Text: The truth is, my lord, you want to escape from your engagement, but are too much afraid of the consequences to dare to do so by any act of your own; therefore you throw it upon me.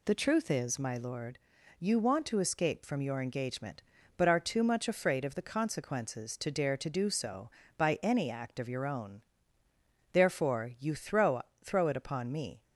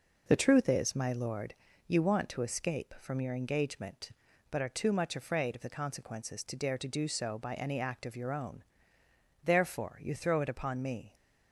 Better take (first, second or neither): second